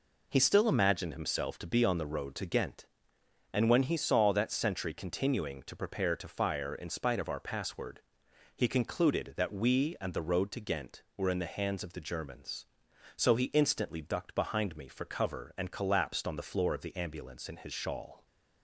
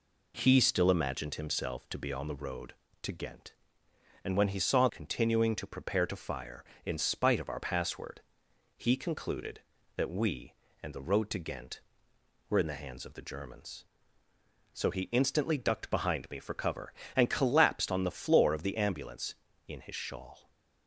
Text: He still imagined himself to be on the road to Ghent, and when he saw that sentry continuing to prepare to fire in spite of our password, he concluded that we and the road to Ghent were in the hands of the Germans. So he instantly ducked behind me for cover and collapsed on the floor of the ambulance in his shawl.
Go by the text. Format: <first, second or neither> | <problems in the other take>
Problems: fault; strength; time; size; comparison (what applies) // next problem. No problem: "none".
first | skips "that sentry"; at 4.8 s